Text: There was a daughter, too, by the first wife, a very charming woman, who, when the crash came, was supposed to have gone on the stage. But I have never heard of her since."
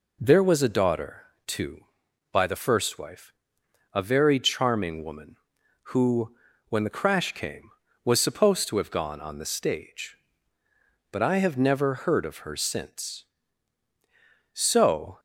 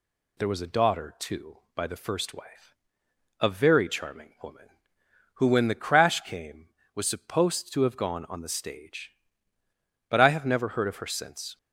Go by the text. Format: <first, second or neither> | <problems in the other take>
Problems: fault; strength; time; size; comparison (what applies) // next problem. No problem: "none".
second | goes on to say "So"; noticeable; from 14.5 s on; 0.68 s long